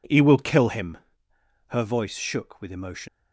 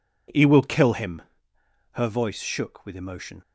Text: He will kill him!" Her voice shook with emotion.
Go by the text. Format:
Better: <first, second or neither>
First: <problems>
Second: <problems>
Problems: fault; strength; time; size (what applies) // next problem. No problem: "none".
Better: second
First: leaves "emotion" unfinished; at 3.0 s; 85 ms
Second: none